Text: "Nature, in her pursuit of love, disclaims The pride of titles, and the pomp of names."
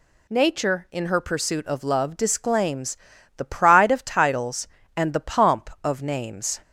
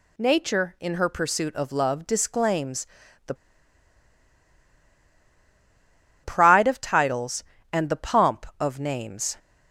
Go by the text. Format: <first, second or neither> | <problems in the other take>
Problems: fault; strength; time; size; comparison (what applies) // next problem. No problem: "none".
first | pauses between "disclaims" and "The"; at 2.8 s; 0.40 s long; also in the first // pauses between "The" and "pride"; strong; at 3.3 s; 2.8 s long